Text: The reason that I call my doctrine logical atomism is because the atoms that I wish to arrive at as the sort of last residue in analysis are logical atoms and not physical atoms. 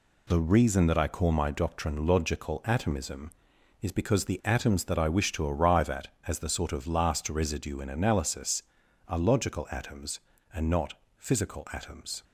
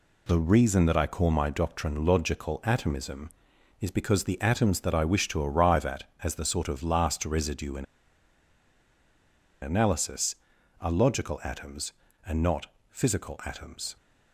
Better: first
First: pauses between "not" and "physical"; slight; at 10.9 s; 0.24 s long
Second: pauses between "in" and "analysis"; strong; at 7.8 s; 1.7 s long // pauses between "not" and "physical"; slight; at 12.6 s; 0.24 s long

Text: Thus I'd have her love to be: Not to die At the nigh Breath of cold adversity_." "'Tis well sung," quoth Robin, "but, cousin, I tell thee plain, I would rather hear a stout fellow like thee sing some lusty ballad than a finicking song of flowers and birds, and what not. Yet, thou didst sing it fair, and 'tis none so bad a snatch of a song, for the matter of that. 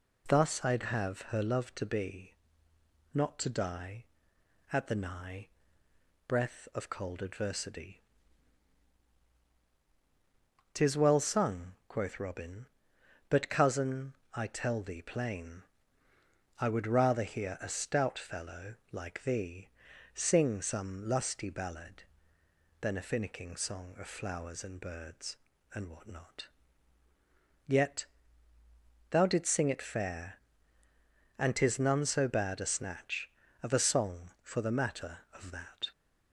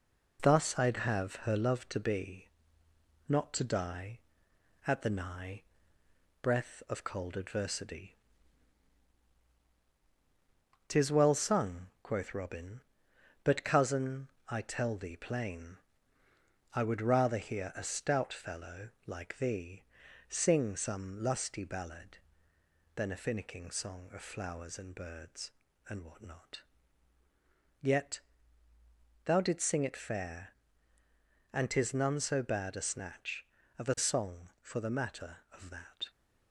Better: first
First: pauses between "nigh" and "Breath"; noticeable; at 5.4 s; 0.78 s long // pauses between "fellow" and "like"; slight; at 18.7 s; 0.18 s long // pauses between "thee" and "sing"; at 19.6 s; 0.44 s long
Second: gets quieter; noticeable; throughout; 4.5 dB // pauses between "nigh" and "Breath"; noticeable; at 5.6 s; 0.78 s long // pauses between "fellow" and "like"; slight; at 18.8 s; 0.18 s long // pauses between "thee" and "sing"; at 19.8 s; 0.44 s long

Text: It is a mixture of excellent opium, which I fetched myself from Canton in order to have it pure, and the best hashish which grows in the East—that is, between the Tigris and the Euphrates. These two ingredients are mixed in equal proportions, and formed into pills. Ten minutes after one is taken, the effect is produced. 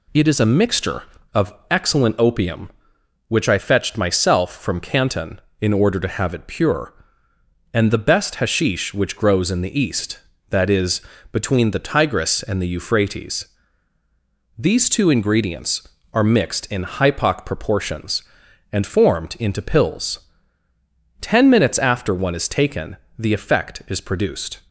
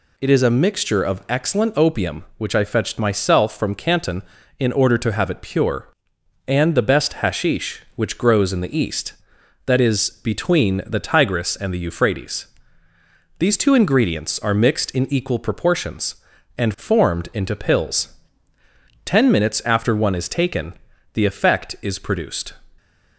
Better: second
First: pauses between "of" and "excellent"; slight; at 1.5 s; 0.18 s long // says "hypoc" for "equal"; at 16.8 s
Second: none

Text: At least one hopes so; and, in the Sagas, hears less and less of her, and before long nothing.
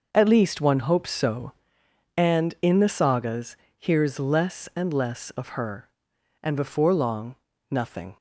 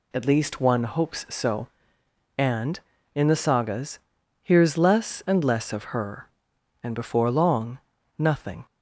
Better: neither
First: pauses between "long" and "nothing"; slight; at 7.3 s; 0.34 s long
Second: pauses between "long" and "nothing"; at 7.7 s; 0.40 s long

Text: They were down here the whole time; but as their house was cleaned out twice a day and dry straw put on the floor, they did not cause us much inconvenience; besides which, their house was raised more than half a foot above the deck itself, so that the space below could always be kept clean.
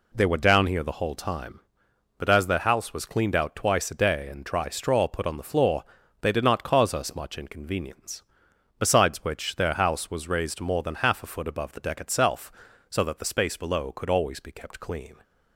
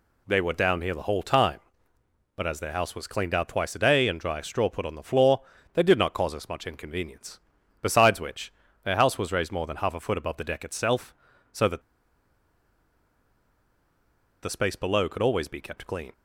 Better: first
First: none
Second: pauses between "that" and "the"; strong; at 11.8 s; 2.6 s long

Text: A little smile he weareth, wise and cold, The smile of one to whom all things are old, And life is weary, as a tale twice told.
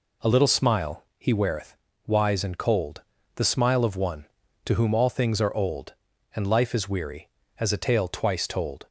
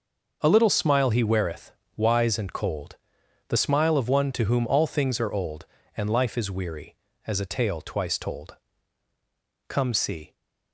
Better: first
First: none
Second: starts louder than the rest; until 1.4 s; 6 dB // goes on to say "Come see"; noticeable; from 9.6 s on; 0.66 s long

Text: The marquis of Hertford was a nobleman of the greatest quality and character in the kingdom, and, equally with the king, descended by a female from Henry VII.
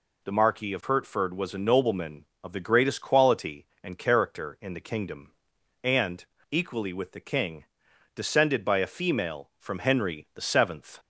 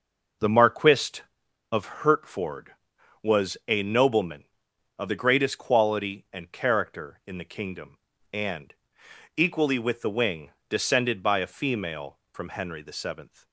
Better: first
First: none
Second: says "wing" for "king"; at 10.1 s

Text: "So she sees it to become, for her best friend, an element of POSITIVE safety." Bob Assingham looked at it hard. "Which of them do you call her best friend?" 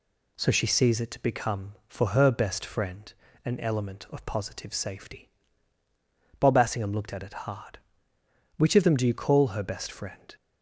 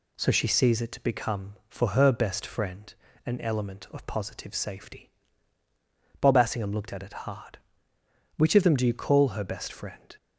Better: neither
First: none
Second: none

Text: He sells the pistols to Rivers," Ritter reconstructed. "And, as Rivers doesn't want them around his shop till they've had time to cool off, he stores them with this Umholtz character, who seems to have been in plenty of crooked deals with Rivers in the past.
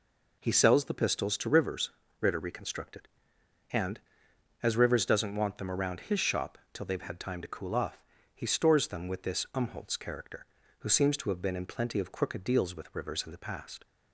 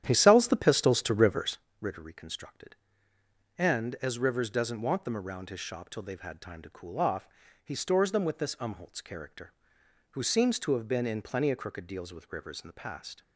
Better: first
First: none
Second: starts louder than the rest; strong; until 1.7 s; 10.5 dB

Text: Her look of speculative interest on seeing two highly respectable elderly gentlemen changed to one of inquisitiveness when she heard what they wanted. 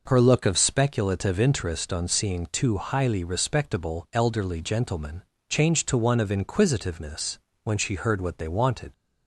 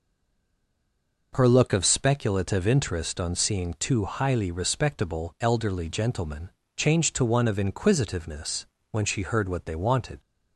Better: first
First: pauses between "gentlemen" and "changed"; slight; at 5.2 s; 0.26 s long // pauses between "inquisitiveness" and "when"; slight; at 7.3 s; 0.26 s long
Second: stays silent before the first word; noticeable; until 1.3 s; 1.3 s long // pauses between "gentlemen" and "changed"; slight; at 6.4 s; 0.26 s long // pauses between "inquisitiveness" and "when"; slight; at 8.6 s; 0.26 s long

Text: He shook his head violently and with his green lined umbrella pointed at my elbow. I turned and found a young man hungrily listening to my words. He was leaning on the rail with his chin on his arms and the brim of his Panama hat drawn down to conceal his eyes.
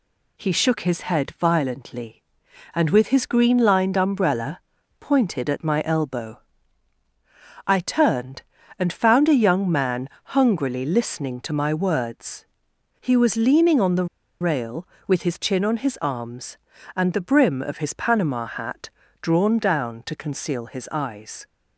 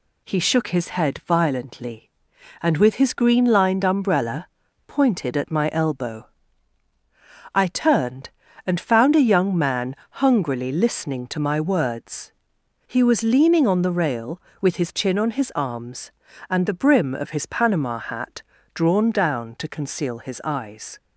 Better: second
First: pauses between "umbrella" and "pointed"; at 4.5 s; 0.40 s long // pauses between "man" and "hungrily"; slight; at 10.0 s; 0.28 s long // pauses between "the" and "rail"; slight; at 14.0 s; 0.35 s long // pauses between "hat" and "drawn"; slight; at 18.9 s; 0.32 s long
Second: pauses between "umbrella" and "pointed"; at 4.4 s; 0.40 s long // pauses between "man" and "hungrily"; slight; at 9.9 s; 0.28 s long // pauses between "hat" and "drawn"; slight; at 18.4 s; 0.32 s long

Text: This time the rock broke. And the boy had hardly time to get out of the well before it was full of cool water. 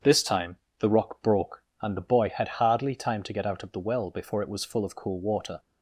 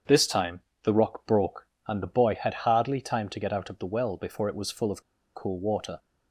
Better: first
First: starts louder than the rest; strong; until 1.2 s; 7.5 dB // pauses between "time" and "the"; slight; at 0.5 s; 0.24 s long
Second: starts louder than the rest; strong; until 1.3 s; 7.5 dB // pauses between "time" and "the"; slight; at 0.6 s; 0.24 s long // pauses between "of" and "cool"; slight; at 5.0 s; 0.33 s long

